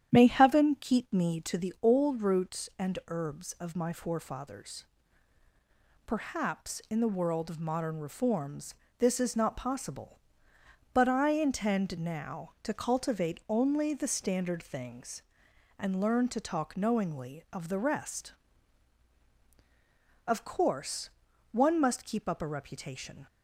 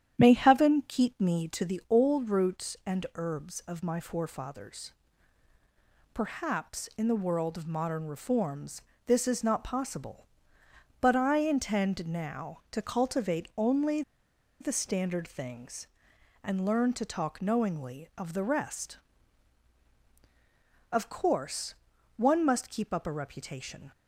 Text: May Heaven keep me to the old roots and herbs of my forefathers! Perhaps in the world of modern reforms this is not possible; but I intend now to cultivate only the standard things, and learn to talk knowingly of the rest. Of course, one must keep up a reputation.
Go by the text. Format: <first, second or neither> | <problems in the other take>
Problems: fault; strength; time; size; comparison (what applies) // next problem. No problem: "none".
first | starts louder than the rest; strong; until 1.2 s; 10 dB; strong in the first // pauses between "reforms" and "this"; slight; at 8.8 s; 0.24 s long; slight in the first // pauses between "only" and "the"; noticeable; at 14.0 s; 0.59 s long